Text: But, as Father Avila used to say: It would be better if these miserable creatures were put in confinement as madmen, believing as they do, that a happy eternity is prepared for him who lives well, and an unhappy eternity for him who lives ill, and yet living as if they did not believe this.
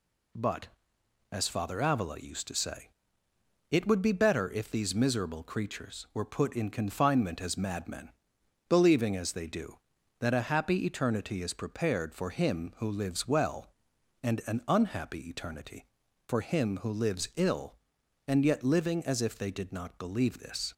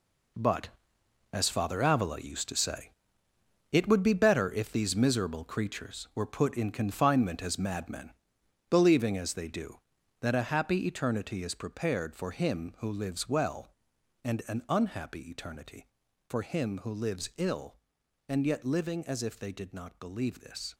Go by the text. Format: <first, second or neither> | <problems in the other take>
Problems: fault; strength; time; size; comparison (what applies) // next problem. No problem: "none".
first | gets quieter; strong; throughout; 10 dB